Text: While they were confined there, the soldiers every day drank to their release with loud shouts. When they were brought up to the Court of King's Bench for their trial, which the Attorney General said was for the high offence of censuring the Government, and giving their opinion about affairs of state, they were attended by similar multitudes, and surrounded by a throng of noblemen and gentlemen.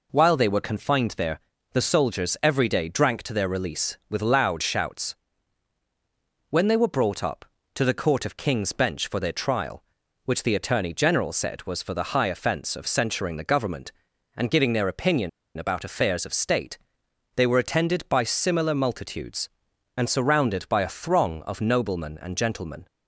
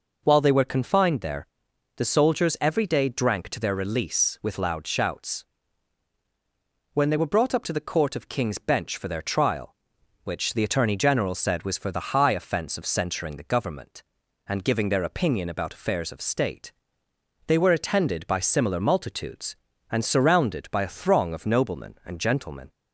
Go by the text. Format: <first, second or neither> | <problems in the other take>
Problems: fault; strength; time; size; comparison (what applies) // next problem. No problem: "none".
second | pauses between "opinion" and "about"; slight; at 15.2 s; 0.28 s long